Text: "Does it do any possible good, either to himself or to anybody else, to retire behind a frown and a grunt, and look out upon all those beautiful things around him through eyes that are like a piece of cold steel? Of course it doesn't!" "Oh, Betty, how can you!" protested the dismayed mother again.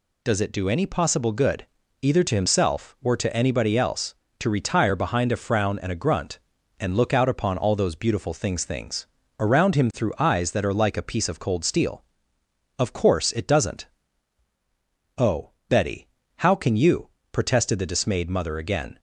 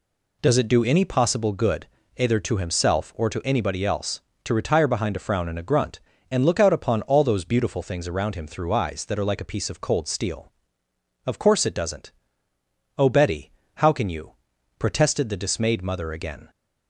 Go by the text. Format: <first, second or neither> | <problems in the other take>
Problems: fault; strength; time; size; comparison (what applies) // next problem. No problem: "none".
second | says "things" twice; at 8.6 s